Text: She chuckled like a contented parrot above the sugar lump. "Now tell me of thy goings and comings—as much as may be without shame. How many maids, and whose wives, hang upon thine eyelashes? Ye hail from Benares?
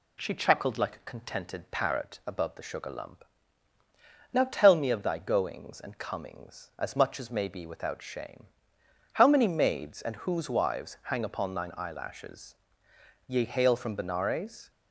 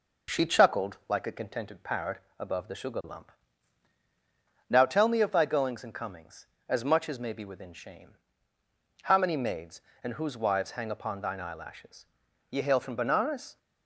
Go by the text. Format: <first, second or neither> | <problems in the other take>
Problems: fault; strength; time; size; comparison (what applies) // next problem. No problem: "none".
first | pauses between "parrot" and "above"; slight; at 2.2 s; 0.16 s long // says "within" for "without"; at 7.4 s